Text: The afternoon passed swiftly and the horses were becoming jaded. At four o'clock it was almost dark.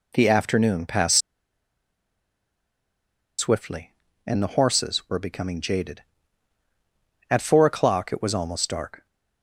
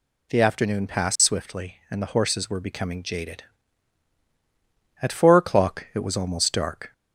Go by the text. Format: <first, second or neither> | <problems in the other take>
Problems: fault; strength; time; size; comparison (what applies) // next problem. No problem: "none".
second | pauses between "passed" and "swiftly"; strong; at 1.1 s; 2.1 s long